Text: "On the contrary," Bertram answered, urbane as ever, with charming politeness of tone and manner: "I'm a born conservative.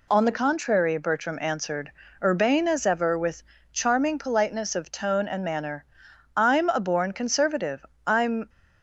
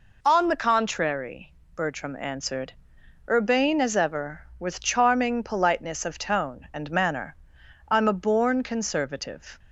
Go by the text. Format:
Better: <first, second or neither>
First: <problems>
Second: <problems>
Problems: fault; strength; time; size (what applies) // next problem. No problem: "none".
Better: second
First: pauses between "with" and "charming"; slight; at 3.4 s; 0.30 s long // goes on to say "I'm"; slight; from 8.0 s on; 0.42 s long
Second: none